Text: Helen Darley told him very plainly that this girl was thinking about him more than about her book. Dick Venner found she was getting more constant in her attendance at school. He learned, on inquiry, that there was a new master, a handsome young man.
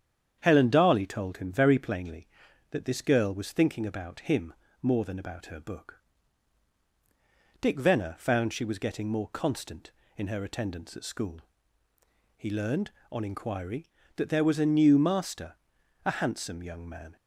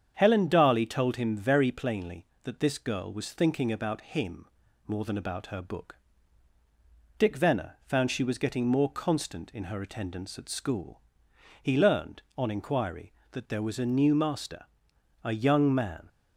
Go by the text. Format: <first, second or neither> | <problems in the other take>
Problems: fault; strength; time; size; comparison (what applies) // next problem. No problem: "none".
first | starts louder than the rest; strong; until 1.1 s; 8 dB; strong in the first // pauses between "him" and "more"; at 4.4 s; 0.42 s long; slight in the first // skips "handsome"; at 15.3 s